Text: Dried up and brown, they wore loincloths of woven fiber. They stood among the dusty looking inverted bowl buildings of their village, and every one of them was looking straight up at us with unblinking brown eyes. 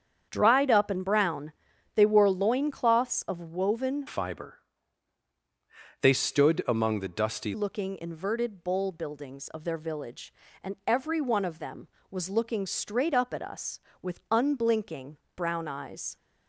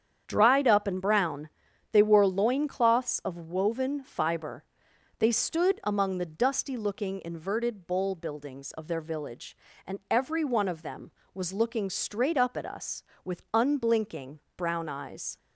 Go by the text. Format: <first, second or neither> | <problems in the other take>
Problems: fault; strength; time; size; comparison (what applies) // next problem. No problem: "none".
second | starts louder than the rest; strong; until 1.3 s; 8 dB; strong in the second // changes voice from "fiber" to "dusty"; from 4.0 to 7.5 s; 3.5 s long // pauses between "unblinking" and "brown"; slight; at 15.1 s; 0.20 s long; slight in the second